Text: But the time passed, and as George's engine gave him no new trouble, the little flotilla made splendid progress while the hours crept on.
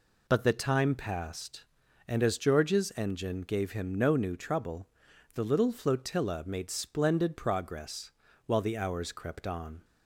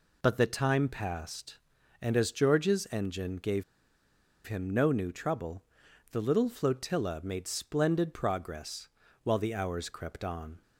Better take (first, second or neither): first